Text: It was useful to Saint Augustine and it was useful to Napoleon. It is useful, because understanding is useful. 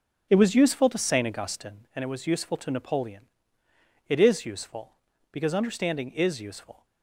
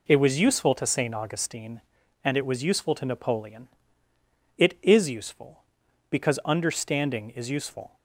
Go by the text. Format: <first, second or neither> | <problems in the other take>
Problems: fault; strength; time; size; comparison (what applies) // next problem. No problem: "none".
second | starts louder than the rest; noticeable; until 1.8 s; 5.5 dB